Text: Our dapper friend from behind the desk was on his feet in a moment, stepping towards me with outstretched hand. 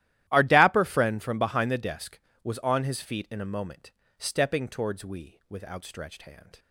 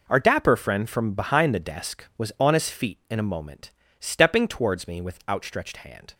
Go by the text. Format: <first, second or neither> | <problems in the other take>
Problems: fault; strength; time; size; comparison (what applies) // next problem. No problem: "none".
second | starts louder than the rest; strong; until 1.2 s; 13.5 dB // says "we" for "me"; at 5.0 s